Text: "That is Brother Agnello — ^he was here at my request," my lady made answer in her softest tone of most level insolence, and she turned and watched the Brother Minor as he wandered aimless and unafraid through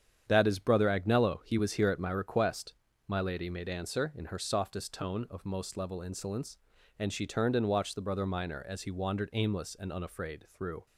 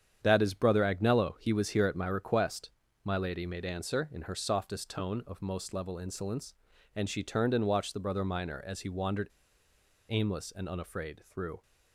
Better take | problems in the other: first | starts louder than the rest; strong; until 1.2 s; 8.5 dB; strong in the first // pauses between "wandered" and "aimless"; noticeable; at 9.2 s; 0.84 s long

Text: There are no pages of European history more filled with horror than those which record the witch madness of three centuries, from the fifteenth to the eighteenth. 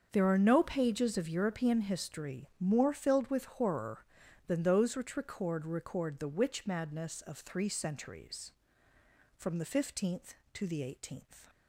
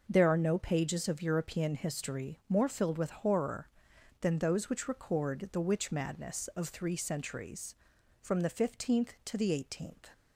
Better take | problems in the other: second | starts louder than the rest; until 1.1 s; 7 dB // says "record" twice; at 5.6 s

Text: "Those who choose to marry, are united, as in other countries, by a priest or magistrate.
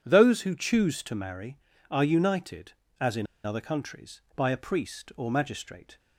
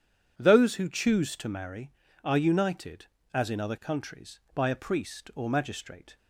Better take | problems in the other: second | starts louder than the rest; strong; until 1.0 s; 9 dB // pauses between "in" and "other"; slight; at 3.2 s; 0.18 s long

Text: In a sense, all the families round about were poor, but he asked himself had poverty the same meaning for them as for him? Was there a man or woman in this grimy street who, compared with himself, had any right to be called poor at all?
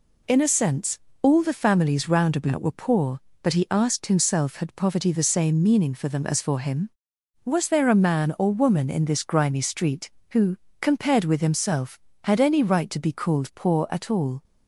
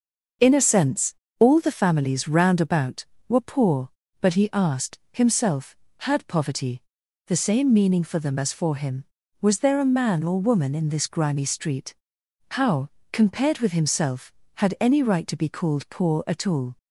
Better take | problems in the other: first | pauses between "poverty" and "the"; noticeable; at 6.8 s; 0.46 s long // says "how" for "who"; at 12.5 s

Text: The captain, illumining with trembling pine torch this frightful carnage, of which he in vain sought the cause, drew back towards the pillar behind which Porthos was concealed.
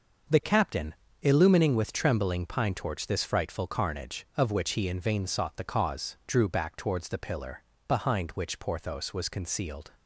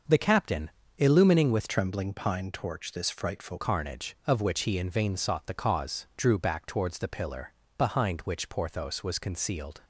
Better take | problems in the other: first | starts louder than the rest; noticeable; until 1.3 s; 6 dB; noticeable in the first // changes voice from "trembling" to "frightful"; from 1.6 to 3.5 s; 1.9 s long // pauses between "pillar" and "behind"; slight; at 7.5 s; 0.26 s long; slight in the first

